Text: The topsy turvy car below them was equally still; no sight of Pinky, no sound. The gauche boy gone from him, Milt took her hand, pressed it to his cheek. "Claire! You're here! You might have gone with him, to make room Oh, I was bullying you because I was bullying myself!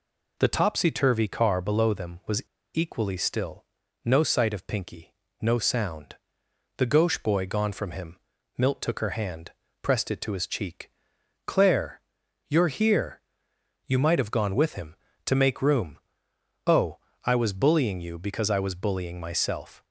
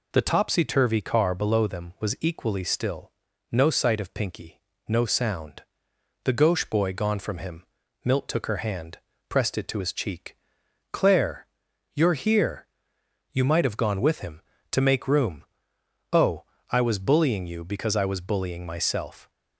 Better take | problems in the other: second | pauses between "was" and "equally"; slight; at 2.4 s; 0.30 s long // pauses between "room" and "Oh"; noticeable; at 15.9 s; 0.68 s long; noticeable in the second

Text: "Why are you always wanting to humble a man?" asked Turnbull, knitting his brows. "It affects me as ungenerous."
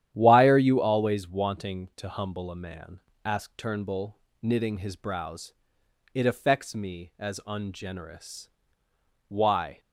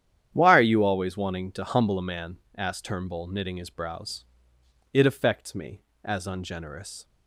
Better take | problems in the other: second | starts louder than the rest; strong; until 1.1 s; 10.5 dB; strong in the second // goes on to say "Why"; from 9.2 s on; 0.52 s long

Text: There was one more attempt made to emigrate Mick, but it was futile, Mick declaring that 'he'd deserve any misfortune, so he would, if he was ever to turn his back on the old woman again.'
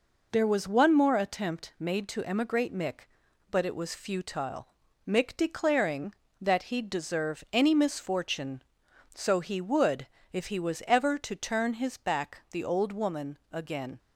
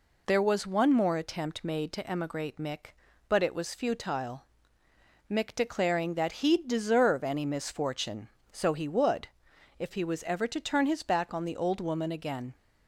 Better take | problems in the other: second | skips "on"; at 12.4 s

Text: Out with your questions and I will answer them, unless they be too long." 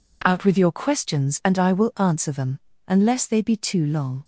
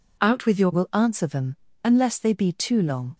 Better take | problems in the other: first | skips "questions and I"; at 0.7 s

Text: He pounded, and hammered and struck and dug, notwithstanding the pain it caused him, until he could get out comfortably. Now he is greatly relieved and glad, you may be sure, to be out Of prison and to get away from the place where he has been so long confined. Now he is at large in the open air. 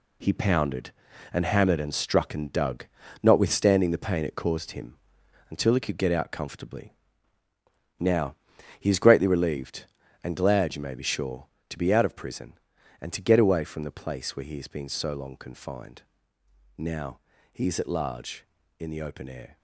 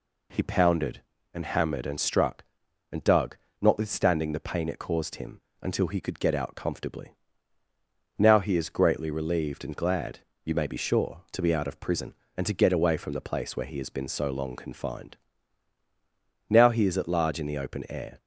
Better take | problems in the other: second | gets quieter; strong; throughout; 9.5 dB // pauses between "Now" and "he"; at 8.3 s; 0.44 s long // pauses between "Now" and "he"; slight; at 17.1 s; 0.30 s long

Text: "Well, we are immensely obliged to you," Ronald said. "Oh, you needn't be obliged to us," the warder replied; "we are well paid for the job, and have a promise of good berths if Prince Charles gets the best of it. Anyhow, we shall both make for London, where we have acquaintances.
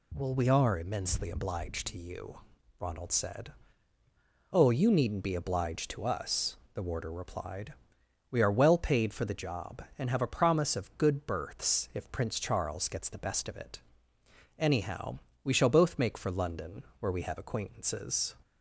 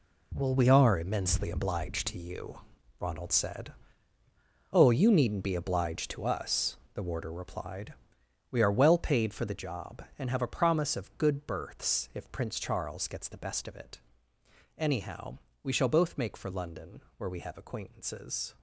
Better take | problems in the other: first | gets quieter; strong; throughout; 10.5 dB

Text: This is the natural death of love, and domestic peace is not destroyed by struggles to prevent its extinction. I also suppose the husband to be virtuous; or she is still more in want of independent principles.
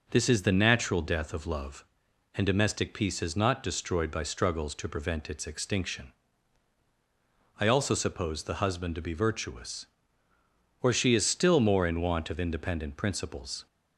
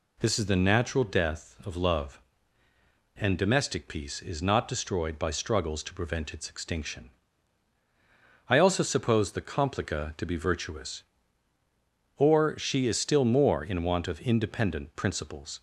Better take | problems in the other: first | says "complica" for "husband"; at 9.4 s

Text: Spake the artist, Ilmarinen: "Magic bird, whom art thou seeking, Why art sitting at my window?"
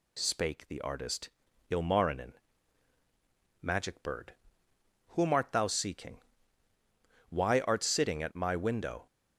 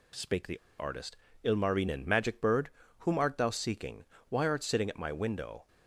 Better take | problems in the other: first | pauses between "the" and "artist"; slight; at 0.5 s; 0.20 s long

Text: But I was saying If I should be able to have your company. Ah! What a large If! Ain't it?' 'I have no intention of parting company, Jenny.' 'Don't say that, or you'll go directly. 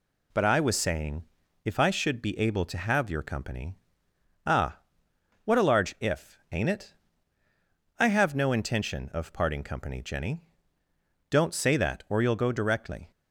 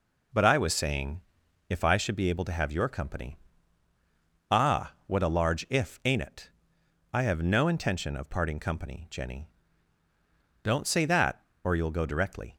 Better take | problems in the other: neither | pauses between "saying" and "If"; the same in both

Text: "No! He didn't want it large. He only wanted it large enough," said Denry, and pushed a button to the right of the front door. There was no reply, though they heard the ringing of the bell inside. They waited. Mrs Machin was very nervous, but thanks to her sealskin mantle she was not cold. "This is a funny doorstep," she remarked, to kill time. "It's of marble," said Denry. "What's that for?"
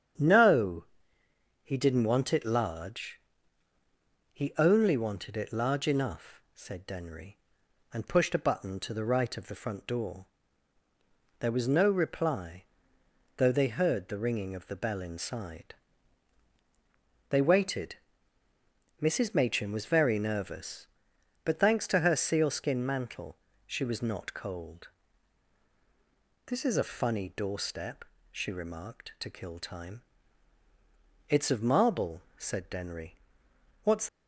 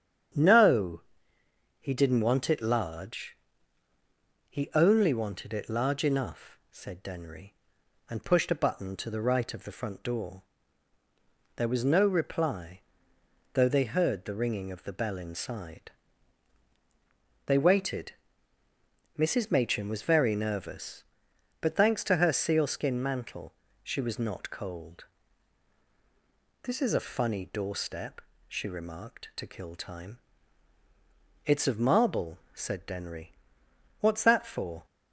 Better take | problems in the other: second | starts louder than the rest; strong; until 1.9 s; 8.5 dB; strong in the second // pauses between "mantle" and "she"; slight; at 23.3 s; 0.30 s long; slight in the second // stops before "that for"; at 34.0 s

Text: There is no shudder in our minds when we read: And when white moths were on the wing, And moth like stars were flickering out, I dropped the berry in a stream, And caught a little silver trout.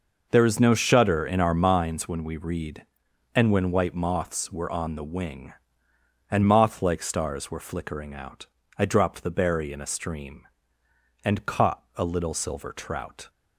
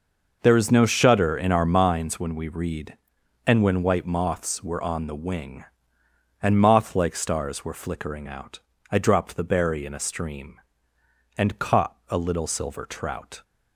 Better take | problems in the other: neither | none

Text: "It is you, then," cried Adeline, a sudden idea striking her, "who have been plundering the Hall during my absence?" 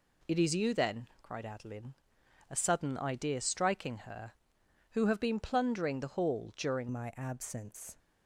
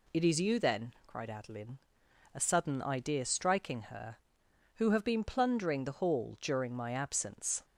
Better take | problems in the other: second | changes voice at "my"; from 6.9 s on; 1.0 s long

